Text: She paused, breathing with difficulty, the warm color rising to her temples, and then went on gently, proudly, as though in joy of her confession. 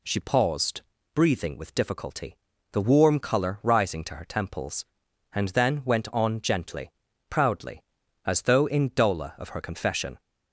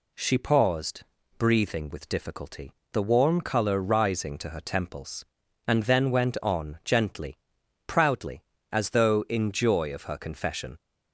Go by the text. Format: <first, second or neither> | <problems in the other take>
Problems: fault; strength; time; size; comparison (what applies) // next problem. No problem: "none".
second | says "dola" for "joy"; at 8.9 s